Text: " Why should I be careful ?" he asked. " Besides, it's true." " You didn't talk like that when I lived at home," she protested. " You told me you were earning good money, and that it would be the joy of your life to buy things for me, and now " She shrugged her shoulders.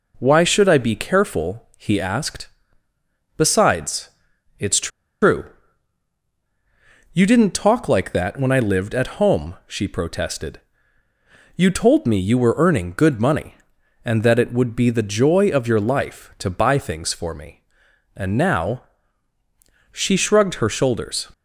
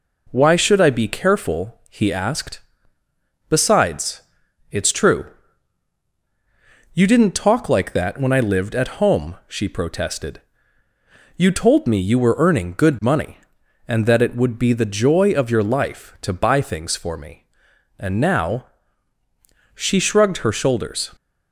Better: second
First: pauses between "it's" and "true"; slight; at 4.8 s; 0.34 s long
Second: none

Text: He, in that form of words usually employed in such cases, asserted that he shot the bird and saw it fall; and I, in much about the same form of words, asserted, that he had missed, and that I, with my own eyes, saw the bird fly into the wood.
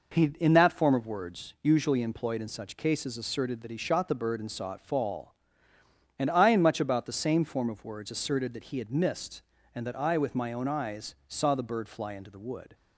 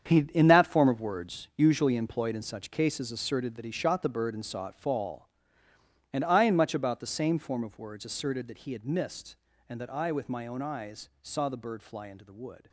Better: first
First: none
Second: gets quieter; strong; throughout; 11.5 dB

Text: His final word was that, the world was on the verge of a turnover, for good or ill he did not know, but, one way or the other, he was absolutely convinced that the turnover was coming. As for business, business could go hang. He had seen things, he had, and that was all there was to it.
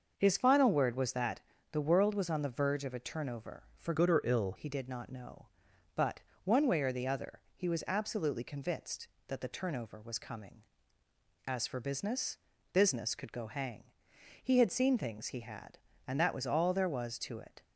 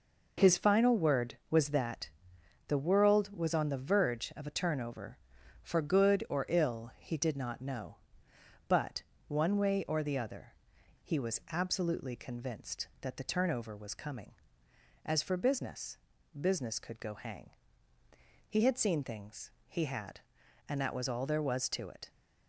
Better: second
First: starts louder than the rest; until 1.1 s; 6 dB // changes voice from "good" to "ill"; from 3.9 to 4.5 s; 0.6 s long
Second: none

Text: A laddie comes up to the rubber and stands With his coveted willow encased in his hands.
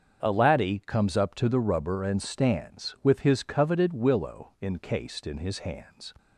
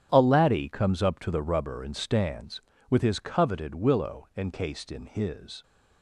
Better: first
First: starts louder than the rest; until 1.2 s; 7 dB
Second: starts louder than the rest; strong; until 1.1 s; 10 dB // stops before "hands"; at 5.6 s

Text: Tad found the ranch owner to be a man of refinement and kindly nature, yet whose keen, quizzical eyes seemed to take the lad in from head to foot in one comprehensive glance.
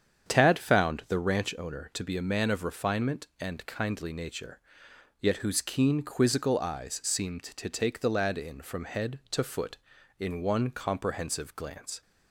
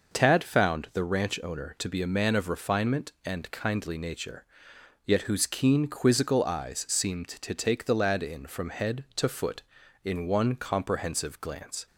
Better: second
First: starts louder than the rest; strong; until 1.5 s; 8 dB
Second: none

